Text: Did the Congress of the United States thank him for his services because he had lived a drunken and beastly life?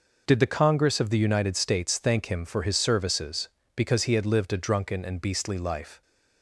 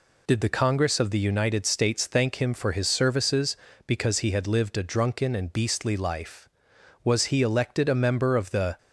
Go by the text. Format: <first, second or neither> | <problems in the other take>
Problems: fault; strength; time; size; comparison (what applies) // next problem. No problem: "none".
first | goes on to say "Was he elected a member of the"; strong; from 7.0 s on; 1.7 s long